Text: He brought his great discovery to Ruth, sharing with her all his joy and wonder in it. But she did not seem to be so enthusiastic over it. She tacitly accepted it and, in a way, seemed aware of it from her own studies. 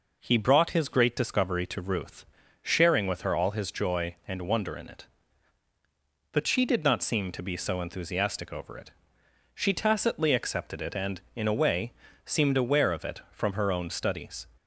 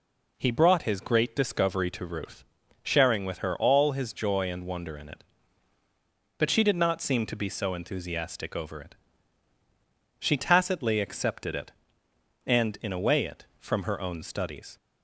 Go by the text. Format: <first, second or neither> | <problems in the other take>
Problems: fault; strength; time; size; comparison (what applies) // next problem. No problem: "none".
first | skips "seemed aware of"; at 13.2 s